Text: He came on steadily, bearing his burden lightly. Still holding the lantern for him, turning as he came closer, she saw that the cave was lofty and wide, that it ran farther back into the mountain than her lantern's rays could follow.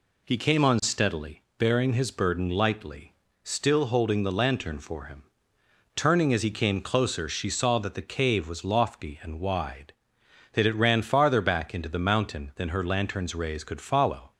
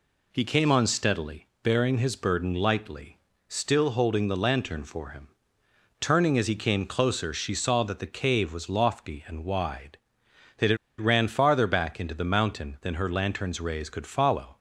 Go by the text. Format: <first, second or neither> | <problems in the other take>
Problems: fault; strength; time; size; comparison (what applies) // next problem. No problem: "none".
first | pauses between "it" and "ran"; slight; at 10.7 s; 0.22 s long